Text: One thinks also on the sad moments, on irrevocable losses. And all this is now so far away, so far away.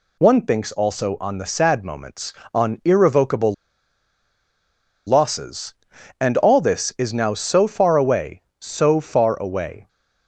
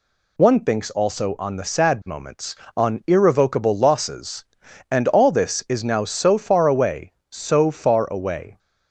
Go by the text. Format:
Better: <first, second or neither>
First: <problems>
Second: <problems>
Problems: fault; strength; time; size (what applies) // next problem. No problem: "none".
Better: second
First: pauses between "irrevocable" and "losses"; strong; at 3.5 s; 1.5 s long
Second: none